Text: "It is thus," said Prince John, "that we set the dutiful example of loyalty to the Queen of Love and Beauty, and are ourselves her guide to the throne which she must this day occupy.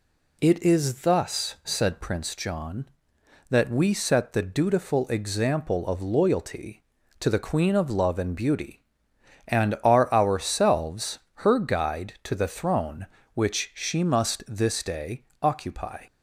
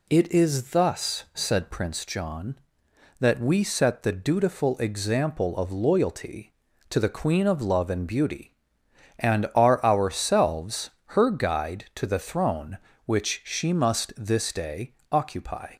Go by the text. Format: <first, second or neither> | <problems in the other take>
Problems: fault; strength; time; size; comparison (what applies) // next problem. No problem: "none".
neither | pauses between "ourselves" and "her"; slight; the same in both // pauses between "day" and "occupy"; slight; the same in both